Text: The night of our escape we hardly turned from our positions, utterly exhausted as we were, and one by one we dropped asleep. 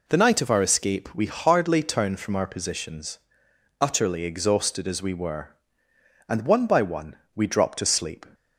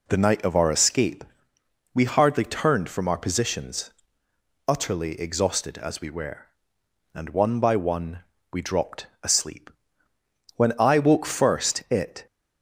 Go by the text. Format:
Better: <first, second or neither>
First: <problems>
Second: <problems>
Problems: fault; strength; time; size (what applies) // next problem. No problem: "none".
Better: first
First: pauses between "one" and "we"; slight; at 7.1 s; 0.18 s long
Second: pauses between "escape" and "we"; noticeable; at 1.2 s; 0.68 s long // pauses between "one" and "we"; slight; at 8.1 s; 0.32 s long // pauses between "dropped" and "asleep"; slight; at 9.0 s; 0.16 s long // goes on to say "When I woke first it"; strong; from 10.5 s on; 1.7 s long